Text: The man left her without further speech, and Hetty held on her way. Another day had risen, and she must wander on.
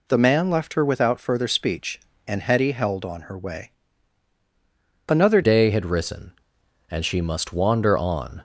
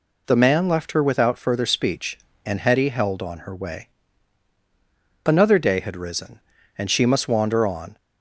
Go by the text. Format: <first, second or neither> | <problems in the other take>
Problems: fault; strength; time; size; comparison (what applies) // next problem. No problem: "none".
second | changes voice at "day"; from 5.4 s on; 3.0 s long